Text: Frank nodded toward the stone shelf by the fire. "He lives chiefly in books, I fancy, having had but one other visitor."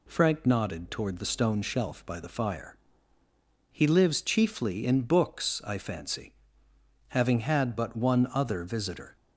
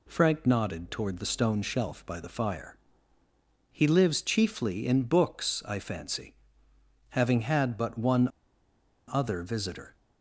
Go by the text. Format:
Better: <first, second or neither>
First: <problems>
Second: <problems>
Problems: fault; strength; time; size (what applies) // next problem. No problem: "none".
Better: first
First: none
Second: pauses between "one" and "other"; noticeable; at 8.2 s; 0.81 s long